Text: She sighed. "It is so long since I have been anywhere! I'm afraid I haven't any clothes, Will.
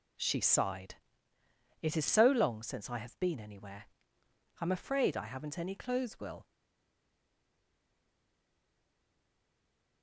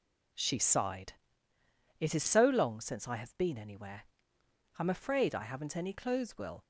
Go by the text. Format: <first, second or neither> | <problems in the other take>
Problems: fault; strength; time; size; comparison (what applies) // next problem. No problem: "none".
second | stays silent after the last word; strong; from 6.4 s on; 3.6 s long